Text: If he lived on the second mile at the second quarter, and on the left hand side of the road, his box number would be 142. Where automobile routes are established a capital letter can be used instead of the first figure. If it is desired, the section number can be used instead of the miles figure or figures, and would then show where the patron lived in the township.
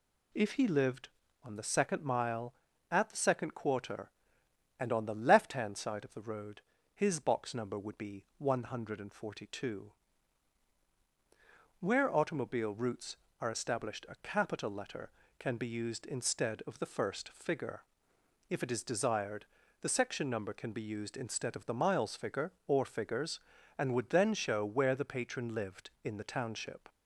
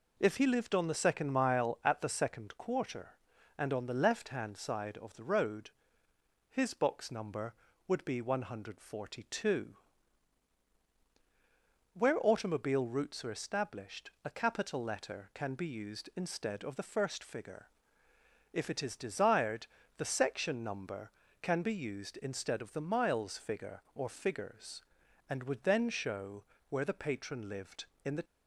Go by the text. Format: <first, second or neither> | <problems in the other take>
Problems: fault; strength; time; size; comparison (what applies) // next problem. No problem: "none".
first | pauses between "established" and "a"; slight; at 14.0 s; 0.16 s long // pauses between "show" and "where"; slight; at 26.4 s; 0.26 s long // stops before "township"; at 28.2 s